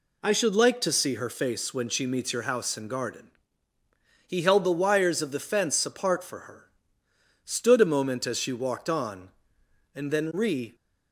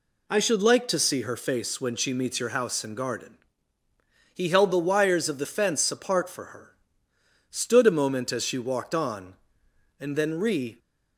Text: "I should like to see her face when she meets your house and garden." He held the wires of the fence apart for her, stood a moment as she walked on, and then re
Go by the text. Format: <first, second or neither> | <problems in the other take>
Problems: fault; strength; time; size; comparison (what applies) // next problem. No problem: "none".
neither | none